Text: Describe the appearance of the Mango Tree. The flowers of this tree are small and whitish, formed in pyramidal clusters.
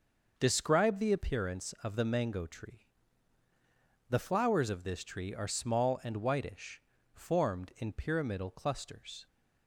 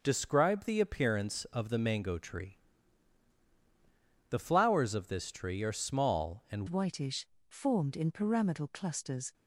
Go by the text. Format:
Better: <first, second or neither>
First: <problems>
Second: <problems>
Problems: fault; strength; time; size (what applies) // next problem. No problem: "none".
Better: first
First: starts louder than the rest; noticeable; until 1.3 s; 6 dB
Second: starts louder than the rest; noticeable; until 1.0 s; 6 dB // changes voice at "whitish"; from 6.6 s on; 2.7 s long